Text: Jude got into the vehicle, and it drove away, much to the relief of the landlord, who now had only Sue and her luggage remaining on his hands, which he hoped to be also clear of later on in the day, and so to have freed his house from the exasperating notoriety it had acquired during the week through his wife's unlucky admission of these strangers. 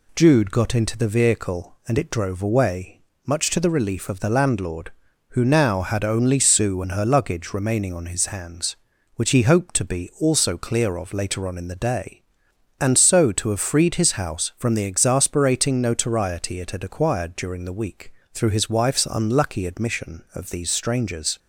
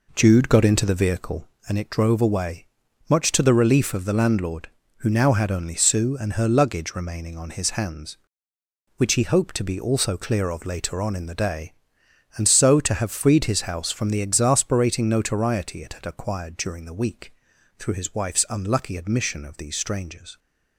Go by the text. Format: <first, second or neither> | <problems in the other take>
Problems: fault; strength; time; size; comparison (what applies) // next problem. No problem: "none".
first | starts louder than the rest; noticeable; until 1.7 s; 4 dB // pauses between "week" and "through"; noticeable; at 17.3 s; 0.46 s long; slight in the first